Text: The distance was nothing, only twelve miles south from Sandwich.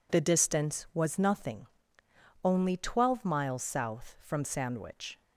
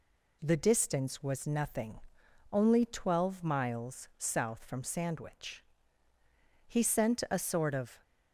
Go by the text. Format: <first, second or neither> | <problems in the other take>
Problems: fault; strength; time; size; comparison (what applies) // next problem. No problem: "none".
first | goes on to say "He sent a sort of"; from 6.6 s on; 1.3 s long